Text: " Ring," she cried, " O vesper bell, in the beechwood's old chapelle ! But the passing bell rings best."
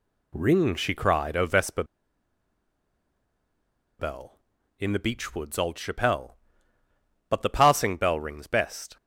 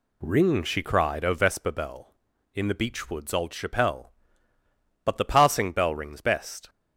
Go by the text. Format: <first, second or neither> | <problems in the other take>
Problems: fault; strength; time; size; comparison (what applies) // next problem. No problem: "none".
second | pauses between "vesper" and "bell"; strong; at 1.8 s; 2.1 s long